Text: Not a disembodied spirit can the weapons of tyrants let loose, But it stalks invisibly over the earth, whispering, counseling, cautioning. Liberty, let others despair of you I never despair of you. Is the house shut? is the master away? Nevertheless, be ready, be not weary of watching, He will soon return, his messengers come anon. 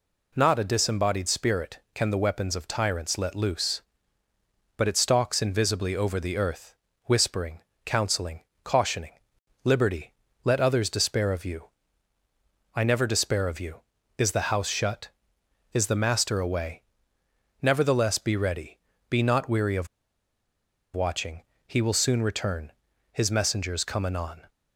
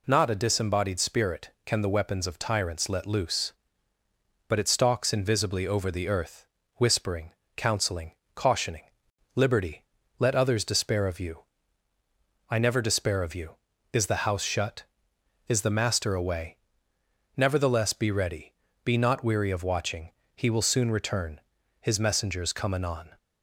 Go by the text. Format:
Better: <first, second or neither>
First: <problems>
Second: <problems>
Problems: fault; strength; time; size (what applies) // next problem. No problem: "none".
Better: second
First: pauses between "you" and "I"; at 11.6 s; 1.0 s long // pauses between "of" and "watching"; at 19.8 s; 1.0 s long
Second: pauses between "you" and "I"; at 11.4 s; 1.0 s long